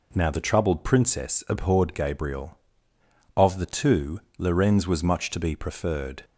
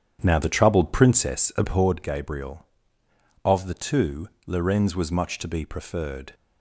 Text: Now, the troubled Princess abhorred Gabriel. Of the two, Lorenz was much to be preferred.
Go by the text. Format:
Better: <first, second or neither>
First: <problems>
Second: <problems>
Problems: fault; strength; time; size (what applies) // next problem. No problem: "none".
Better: first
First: none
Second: starts louder than the rest; strong; until 2.0 s; 9.5 dB